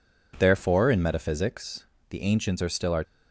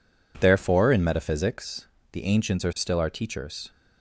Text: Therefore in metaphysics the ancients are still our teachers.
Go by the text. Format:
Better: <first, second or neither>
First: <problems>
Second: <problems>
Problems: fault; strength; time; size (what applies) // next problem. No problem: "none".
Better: second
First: pauses between "metaphysics" and "the"; slight; at 1.8 s; 0.25 s long // stops before "teachers"; at 3.0 s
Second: pauses between "metaphysics" and "the"; slight; at 1.8 s; 0.26 s long